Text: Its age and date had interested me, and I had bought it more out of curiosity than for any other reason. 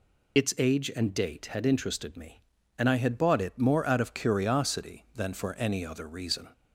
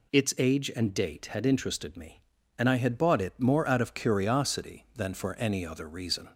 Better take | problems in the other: second | loses the start of "Its"; at 0.3 s; 50 ms

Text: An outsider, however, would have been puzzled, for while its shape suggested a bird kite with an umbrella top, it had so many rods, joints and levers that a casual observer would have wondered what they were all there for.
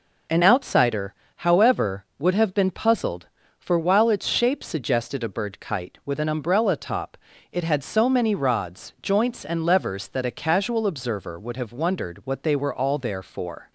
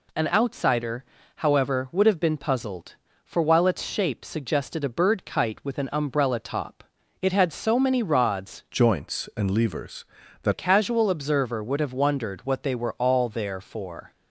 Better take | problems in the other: first | changes voice from "joints" to "that"; from 8.7 to 10.5 s; 1.8 s long

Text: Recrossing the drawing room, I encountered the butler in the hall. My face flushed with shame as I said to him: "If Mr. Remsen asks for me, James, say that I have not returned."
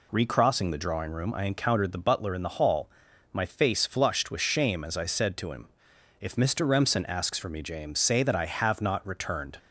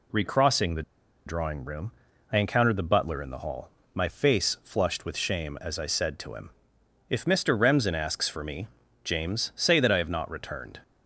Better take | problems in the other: first | pauses between "the" and "drawing"; at 0.8 s; 0.43 s long

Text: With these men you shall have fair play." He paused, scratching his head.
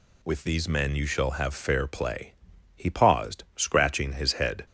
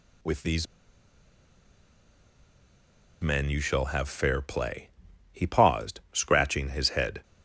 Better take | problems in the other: first | pauses between "these" and "men"; strong; at 0.6 s; 2.5 s long

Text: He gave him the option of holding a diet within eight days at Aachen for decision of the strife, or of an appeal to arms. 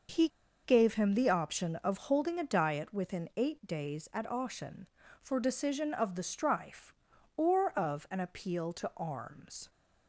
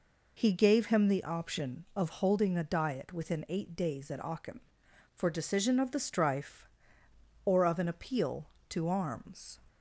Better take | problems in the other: second | starts louder than the rest; noticeable; until 1.4 s; 6 dB // pauses between "He" and "gave"; at 0.2 s; 0.36 s long

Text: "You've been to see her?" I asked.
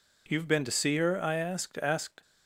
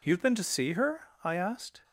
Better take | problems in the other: second | says "asked" twice; at 1.7 s

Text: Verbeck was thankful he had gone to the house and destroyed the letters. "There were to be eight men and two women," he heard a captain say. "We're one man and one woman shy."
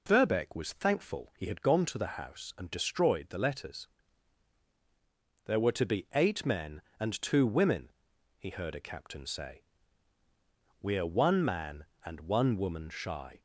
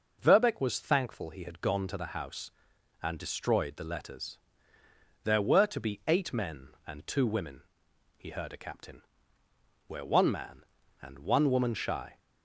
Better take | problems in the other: first | skips "say"; at 9.4 s

